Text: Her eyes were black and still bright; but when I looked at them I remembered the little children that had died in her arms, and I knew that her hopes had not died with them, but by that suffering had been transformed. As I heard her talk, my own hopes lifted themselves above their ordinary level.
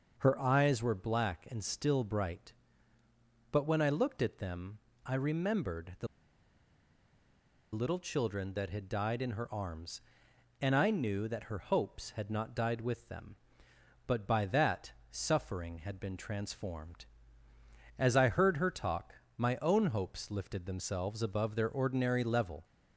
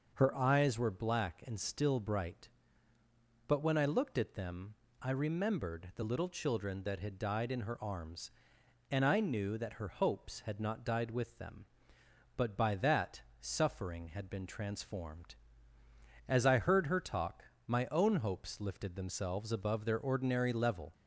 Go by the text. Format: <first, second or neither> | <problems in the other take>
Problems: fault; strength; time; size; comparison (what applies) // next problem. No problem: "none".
second | pauses between "them" and "I"; slight; at 4.7 s; 0.26 s long; slight in the second // pauses between "the" and "little"; strong; at 6.0 s; 1.6 s long // pauses between "that" and "suffering"; slight; at 14.9 s; 0.18 s long; slight in the second